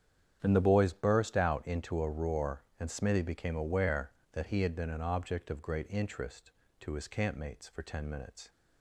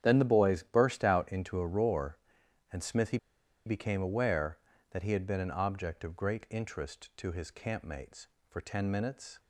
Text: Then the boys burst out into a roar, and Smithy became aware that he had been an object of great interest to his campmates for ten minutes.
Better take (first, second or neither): first